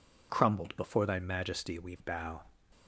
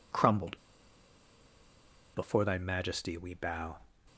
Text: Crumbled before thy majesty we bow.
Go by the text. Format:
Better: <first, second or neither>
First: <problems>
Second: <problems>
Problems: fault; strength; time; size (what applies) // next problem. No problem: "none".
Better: first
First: none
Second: pauses between "Crumbled" and "before"; strong; at 0.5 s; 1.5 s long